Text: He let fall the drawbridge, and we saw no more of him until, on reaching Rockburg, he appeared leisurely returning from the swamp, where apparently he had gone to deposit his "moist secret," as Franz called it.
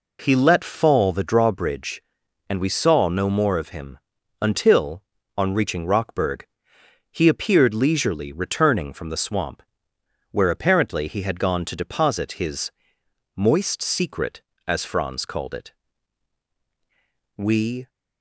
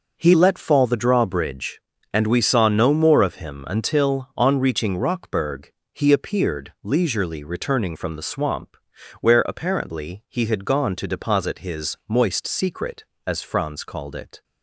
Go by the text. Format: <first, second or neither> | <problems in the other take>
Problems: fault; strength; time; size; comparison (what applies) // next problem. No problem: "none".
second | pauses between "him" and "until"; noticeable; at 3.9 s; 0.46 s long // pauses between "his" and "moist"; noticeable; at 12.7 s; 0.66 s long // goes on to say "We"; from 17.3 s on; 0.52 s long